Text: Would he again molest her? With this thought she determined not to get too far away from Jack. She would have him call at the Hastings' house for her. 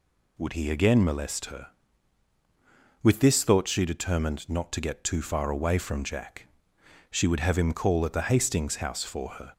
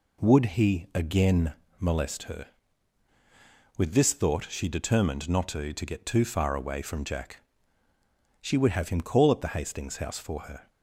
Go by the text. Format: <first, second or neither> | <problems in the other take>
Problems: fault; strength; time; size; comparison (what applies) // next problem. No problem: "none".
first | pauses between "again" and "molest"; slight; at 1.5 s; 0.26 s long // says "to" twice; at 5.7 s